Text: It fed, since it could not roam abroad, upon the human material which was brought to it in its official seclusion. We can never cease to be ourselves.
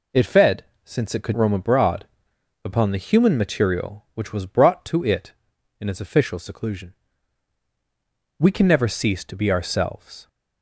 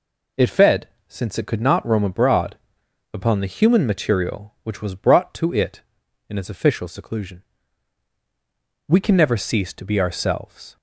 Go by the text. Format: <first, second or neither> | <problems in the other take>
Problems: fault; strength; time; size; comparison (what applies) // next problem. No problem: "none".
second | skips "not"; at 1.3 s